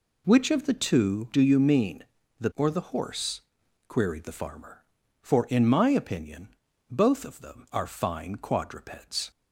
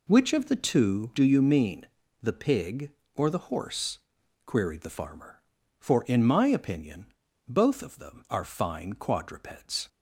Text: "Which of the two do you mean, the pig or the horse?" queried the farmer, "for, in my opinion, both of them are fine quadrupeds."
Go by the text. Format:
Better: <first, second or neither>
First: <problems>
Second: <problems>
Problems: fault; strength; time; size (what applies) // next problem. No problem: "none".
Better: second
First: skips "pig"; at 2.5 s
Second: none